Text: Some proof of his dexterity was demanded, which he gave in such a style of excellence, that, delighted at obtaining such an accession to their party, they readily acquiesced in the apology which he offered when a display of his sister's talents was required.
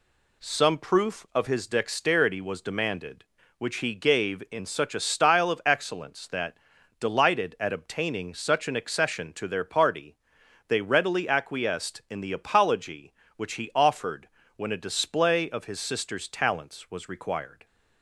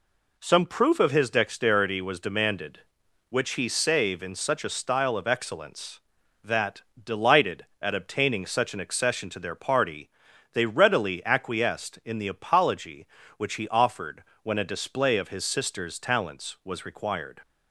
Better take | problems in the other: first | says "save" for "gave"; at 3.6 s // pauses between "offered" and "when"; slight; at 14.2 s; 0.20 s long; slight in the first

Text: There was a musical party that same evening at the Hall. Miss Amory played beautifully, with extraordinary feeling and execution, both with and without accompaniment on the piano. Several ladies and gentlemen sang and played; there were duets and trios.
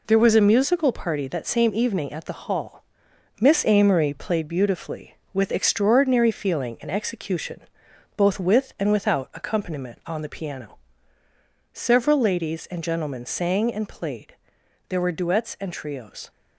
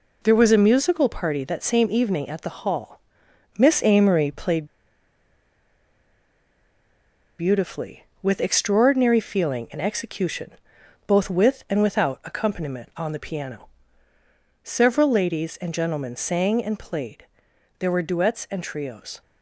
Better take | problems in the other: first | pauses between "played" and "beautifully"; strong; at 4.6 s; 2.7 s long

